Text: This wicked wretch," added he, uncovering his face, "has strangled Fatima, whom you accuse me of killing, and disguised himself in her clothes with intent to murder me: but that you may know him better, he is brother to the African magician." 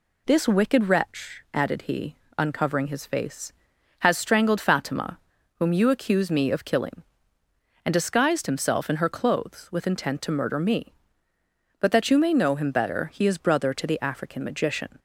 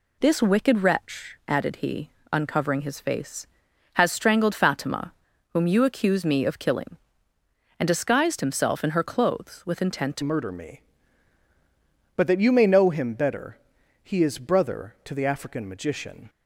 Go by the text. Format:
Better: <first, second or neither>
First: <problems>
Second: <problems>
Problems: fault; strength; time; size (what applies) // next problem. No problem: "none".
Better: first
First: none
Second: changes voice at "murder"; from 10.2 s on; 6.0 s long